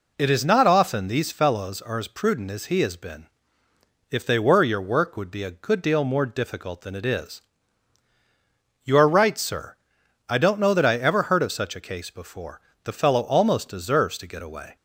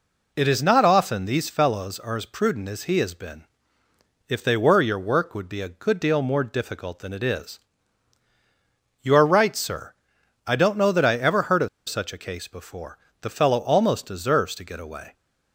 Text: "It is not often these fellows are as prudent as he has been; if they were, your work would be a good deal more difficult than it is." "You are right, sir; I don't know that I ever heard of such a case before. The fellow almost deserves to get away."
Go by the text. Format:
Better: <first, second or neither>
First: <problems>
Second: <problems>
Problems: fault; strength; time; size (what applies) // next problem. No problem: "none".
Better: first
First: none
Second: pauses between "of" and "such"; slight; at 11.6 s; 0.20 s long